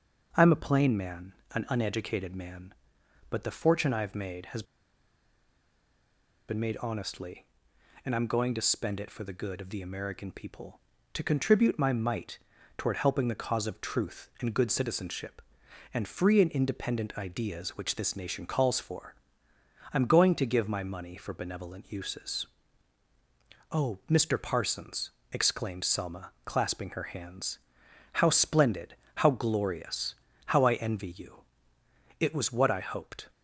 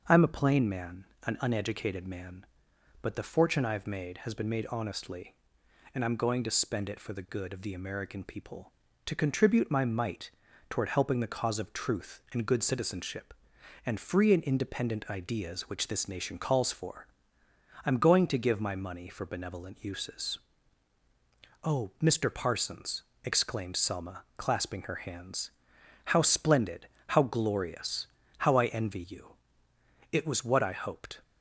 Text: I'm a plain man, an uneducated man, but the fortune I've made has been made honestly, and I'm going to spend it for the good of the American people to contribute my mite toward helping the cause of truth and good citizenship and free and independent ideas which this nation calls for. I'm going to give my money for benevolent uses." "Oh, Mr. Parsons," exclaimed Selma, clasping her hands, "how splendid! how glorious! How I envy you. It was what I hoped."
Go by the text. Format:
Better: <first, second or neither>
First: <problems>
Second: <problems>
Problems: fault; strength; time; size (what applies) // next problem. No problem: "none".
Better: second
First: starts louder than the rest; until 1.3 s; 6.5 dB // pauses between "has" and "been"; strong; at 4.6 s; 1.8 s long // pauses between "mite" and "toward"; at 12.3 s; 0.40 s long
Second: starts louder than the rest; until 1.0 s; 6.5 dB // pauses between "mite" and "toward"; at 10.2 s; 0.40 s long